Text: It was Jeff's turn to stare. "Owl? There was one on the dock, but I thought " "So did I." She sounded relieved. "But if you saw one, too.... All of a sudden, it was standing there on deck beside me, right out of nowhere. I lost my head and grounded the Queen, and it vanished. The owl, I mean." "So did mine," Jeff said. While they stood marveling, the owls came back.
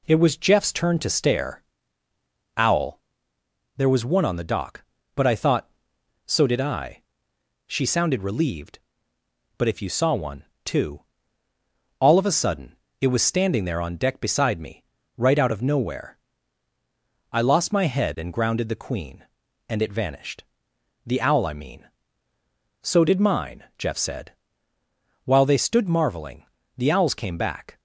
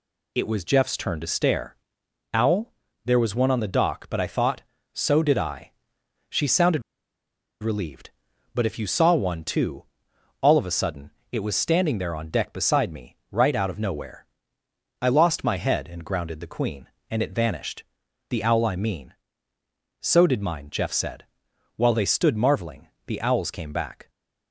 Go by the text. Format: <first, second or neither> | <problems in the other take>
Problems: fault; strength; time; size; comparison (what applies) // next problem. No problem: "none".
first | pauses between "sounded" and "relieved"; noticeable; at 6.8 s; 0.81 s long